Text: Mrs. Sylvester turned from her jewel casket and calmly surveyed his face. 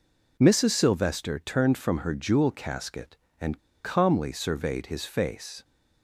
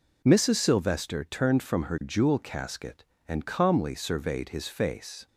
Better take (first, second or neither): second